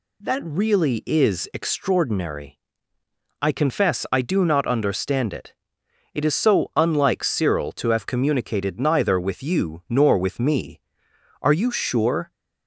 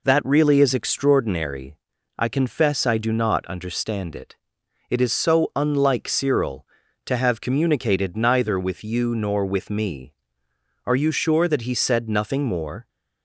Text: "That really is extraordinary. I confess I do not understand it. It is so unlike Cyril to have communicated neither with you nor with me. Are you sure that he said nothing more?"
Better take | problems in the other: second | stops before "that he said nothing more"; at 12.3 s

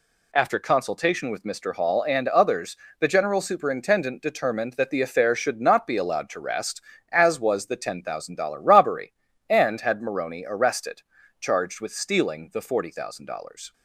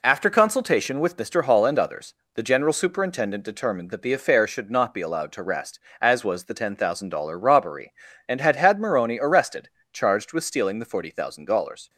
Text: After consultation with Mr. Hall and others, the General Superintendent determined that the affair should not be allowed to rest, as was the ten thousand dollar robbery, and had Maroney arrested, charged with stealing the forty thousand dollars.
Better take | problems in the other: first | says "had" twice; at 8.5 s

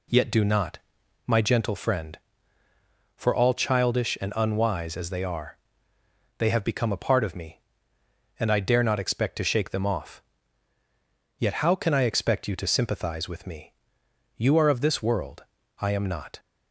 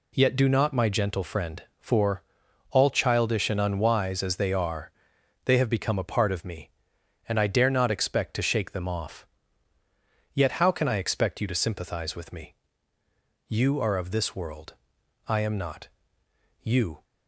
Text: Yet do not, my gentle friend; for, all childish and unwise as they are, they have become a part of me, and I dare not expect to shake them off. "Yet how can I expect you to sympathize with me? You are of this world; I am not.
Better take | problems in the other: first | goes on to say "You"; slight; from 16.6 s on; 0.42 s long

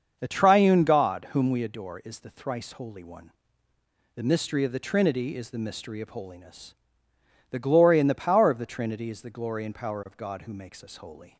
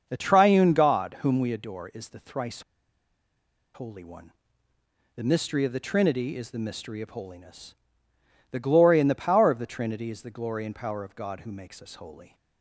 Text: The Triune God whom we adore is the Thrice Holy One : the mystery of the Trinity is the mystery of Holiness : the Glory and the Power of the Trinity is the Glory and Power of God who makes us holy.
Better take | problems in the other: first | starts louder than the rest; until 1.0 s; 6.5 dB; also in the first // pauses between "Thrice" and "Holy"; at 2.6 s; 1.1 s long

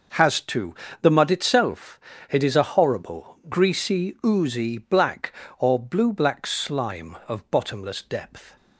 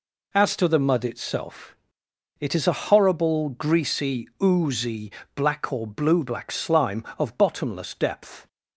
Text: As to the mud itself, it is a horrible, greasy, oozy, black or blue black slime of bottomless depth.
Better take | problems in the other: second | says "Has" for "As"; at 0.1 s // pauses between "to" and "the"; slight; at 0.7 s; 0.28 s long

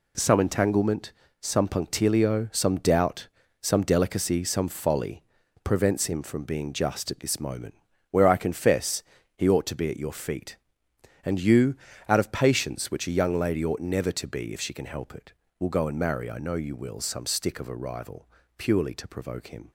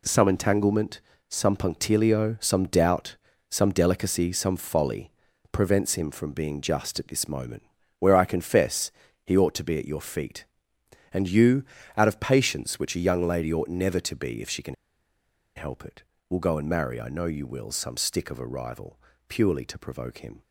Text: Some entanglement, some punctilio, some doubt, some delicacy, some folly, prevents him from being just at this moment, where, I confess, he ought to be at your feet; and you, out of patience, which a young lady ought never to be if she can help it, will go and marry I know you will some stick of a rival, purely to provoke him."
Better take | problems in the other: first | pauses between "can" and "help"; noticeable; at 14.7 s; 0.81 s long

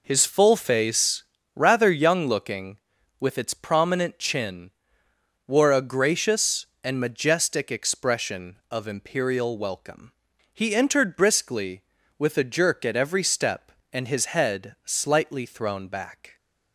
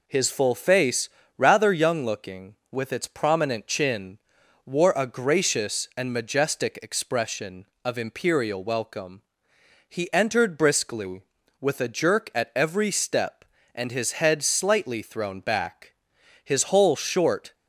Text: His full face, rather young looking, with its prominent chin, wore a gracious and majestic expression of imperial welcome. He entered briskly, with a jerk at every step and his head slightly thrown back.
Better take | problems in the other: first | goes on to say "His whole short"; noticeable; from 16.4 s on; 1.1 s long

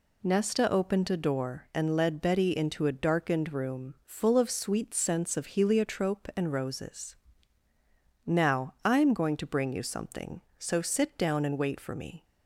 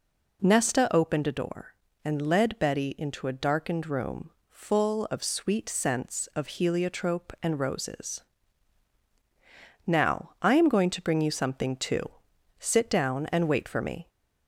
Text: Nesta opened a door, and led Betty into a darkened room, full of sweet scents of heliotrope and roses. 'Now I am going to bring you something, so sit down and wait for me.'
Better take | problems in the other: first | says "too" for "so"; at 11.7 s

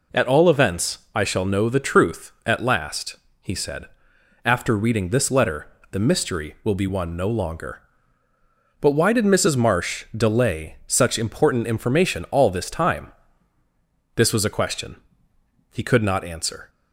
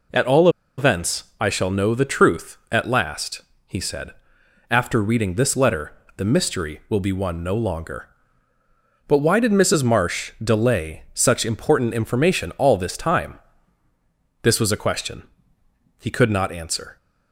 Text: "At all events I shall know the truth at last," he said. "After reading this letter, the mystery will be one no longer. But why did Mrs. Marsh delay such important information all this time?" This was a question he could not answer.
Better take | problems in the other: first | pauses between "all" and "events"; slight; at 0.4 s; 0.29 s long // pauses between "question" and "he"; noticeable; at 15.2 s; 0.78 s long; noticeable in the first

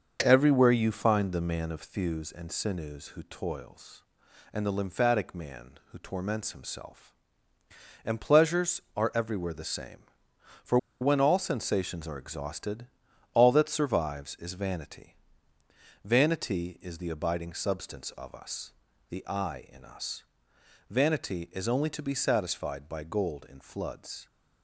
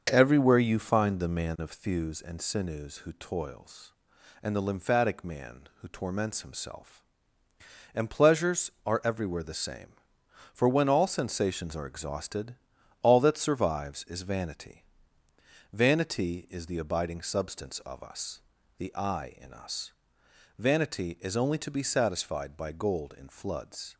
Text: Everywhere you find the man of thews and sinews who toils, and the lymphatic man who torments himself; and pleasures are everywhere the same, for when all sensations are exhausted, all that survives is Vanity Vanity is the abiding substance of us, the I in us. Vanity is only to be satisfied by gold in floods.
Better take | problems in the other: second | starts louder than the rest; until 1.2 s; 6.5 dB; also in the second // pauses between "for" and "when"; slight; at 10.7 s; 0.23 s long // pauses between "Vanity" and "Vanity"; noticeable; at 15.1 s; 0.88 s long; noticeable in the second

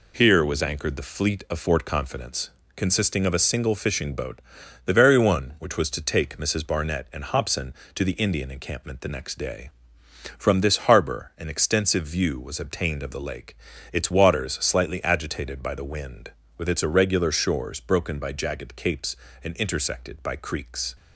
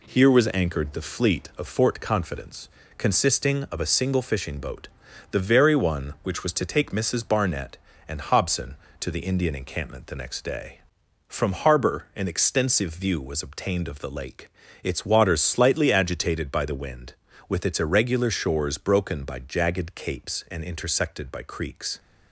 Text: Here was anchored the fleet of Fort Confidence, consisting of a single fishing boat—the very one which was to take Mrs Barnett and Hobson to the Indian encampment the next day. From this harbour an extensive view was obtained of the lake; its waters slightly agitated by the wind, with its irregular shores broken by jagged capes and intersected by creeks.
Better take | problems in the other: first | skips "this"; at 11.5 s

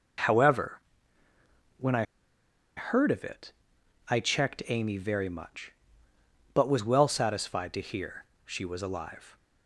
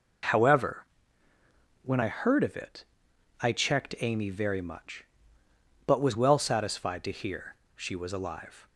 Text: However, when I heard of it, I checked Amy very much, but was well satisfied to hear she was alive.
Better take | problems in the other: second | pauses between "I" and "heard"; noticeable; at 2.0 s; 0.73 s long // pauses between "hear" and "she"; slight; at 8.2 s; 0.20 s long; slight in the second

